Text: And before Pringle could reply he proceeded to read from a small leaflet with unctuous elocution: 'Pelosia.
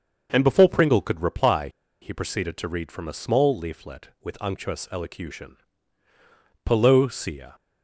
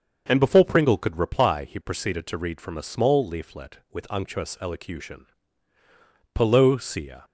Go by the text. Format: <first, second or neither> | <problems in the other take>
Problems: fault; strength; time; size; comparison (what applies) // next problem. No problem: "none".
second | starts louder than the rest; until 1.3 s; 6.5 dB; also in the second // pauses between "reply" and "he"; slight; at 1.6 s; 0.32 s long